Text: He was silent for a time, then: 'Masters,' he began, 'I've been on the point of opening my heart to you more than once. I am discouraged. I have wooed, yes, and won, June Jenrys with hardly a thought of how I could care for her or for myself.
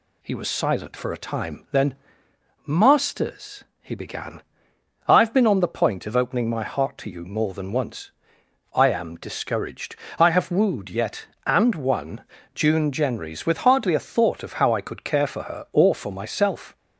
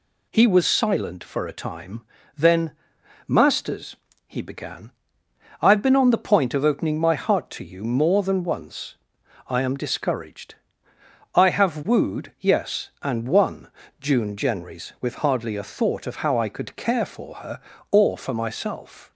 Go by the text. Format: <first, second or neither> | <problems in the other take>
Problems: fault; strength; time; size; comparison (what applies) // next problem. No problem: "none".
second | says "yet" for "yes"; at 10.9 s